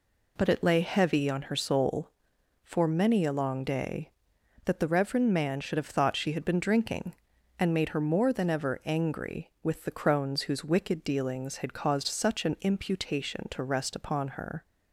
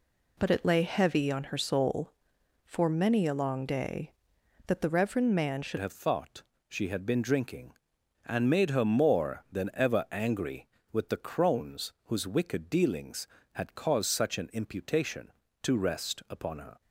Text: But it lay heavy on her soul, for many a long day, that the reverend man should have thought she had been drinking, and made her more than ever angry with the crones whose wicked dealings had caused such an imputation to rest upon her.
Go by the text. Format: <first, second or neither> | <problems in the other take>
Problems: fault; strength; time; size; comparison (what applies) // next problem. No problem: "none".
first | changes voice at "have"; from 5.7 s on; 11.1 s long // pauses between "thought" and "she"; slight; at 6.4 s; 0.26 s long